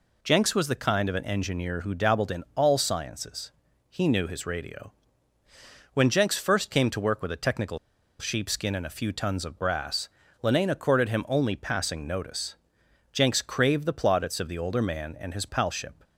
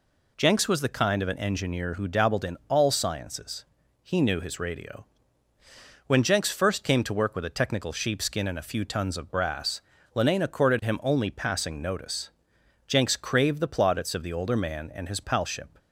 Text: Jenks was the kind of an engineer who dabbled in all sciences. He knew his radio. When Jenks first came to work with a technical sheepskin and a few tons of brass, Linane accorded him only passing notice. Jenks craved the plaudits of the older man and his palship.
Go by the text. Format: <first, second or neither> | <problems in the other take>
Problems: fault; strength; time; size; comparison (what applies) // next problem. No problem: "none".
second | pauses between "technical" and "sheepskin"; at 7.7 s; 0.41 s long